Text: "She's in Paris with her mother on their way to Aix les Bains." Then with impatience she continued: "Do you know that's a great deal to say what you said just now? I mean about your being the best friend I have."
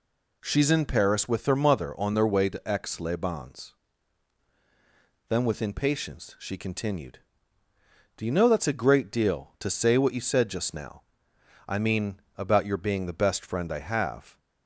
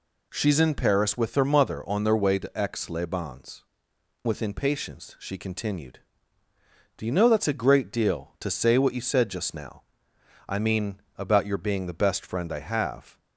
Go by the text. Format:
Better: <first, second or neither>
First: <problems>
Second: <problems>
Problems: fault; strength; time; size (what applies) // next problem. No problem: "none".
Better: first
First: pauses between "mean" and "about"; slight; at 12.2 s; 0.16 s long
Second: skips "Then"; at 3.9 s // pauses between "mean" and "about"; slight; at 11.0 s; 0.16 s long